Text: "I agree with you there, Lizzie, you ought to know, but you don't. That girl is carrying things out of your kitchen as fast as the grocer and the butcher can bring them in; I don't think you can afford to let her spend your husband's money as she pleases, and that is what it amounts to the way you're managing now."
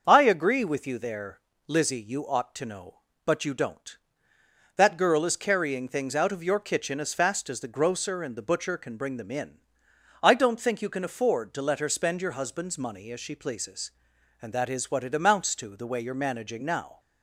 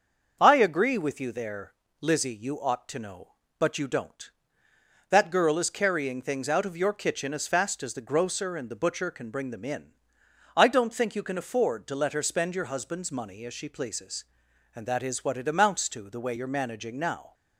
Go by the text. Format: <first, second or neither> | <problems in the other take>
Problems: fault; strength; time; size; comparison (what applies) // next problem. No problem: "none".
neither | starts louder than the rest; the same in both